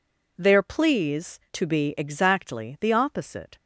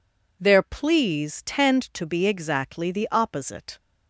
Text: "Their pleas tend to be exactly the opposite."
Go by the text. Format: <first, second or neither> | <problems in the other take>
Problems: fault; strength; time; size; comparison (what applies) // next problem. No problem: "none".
second | skips "tend"; at 1.4 s